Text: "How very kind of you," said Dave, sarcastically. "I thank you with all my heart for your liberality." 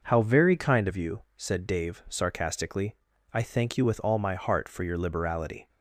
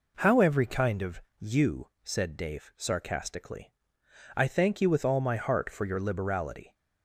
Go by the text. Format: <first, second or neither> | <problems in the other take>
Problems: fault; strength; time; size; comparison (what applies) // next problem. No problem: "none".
first | says "every" for "very"; at 0.3 s // pauses between "of" and "you"; slight; at 1.2 s; 0.18 s long